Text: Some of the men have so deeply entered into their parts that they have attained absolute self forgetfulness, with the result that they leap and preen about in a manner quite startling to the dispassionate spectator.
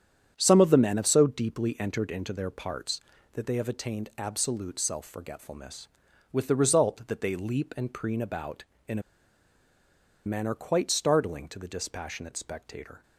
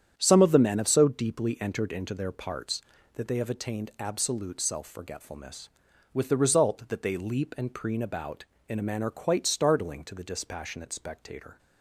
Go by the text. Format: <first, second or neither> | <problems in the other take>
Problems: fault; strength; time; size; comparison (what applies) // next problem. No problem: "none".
second | starts louder than the rest; strong; until 1.3 s; 8.5 dB; strong in the second // pauses between "a" and "manner"; at 9.0 s; 1.2 s long